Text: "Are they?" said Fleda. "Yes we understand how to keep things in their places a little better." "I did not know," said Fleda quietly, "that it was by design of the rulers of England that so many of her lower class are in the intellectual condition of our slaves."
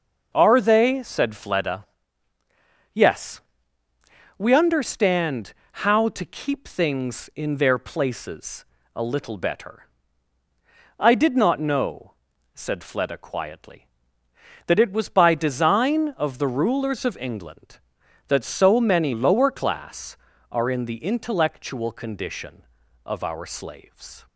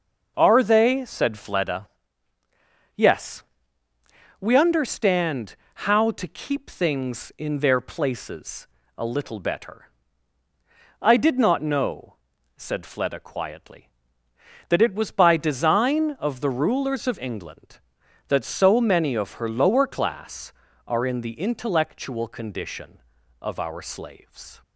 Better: second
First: pauses between "Yes" and "we"; noticeable; at 3.3 s; 0.98 s long // pauses between "understand" and "how"; slight; at 5.5 s; 0.32 s long // pauses between "places" and "a"; slight; at 8.6 s; 0.32 s long // skips "of her"; at 19.1 s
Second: pauses between "Yes" and "we"; noticeable; at 3.4 s; 0.98 s long // pauses between "understand" and "how"; slight; at 5.5 s; 0.32 s long // pauses between "places" and "a"; slight; at 8.6 s; 0.32 s long

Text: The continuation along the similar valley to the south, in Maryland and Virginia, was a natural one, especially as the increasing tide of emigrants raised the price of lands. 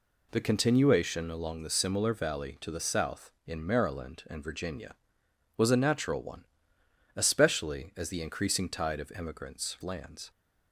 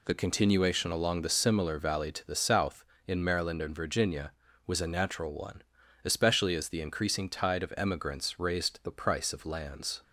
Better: second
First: skips "raised the price of"; at 9.7 s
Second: none

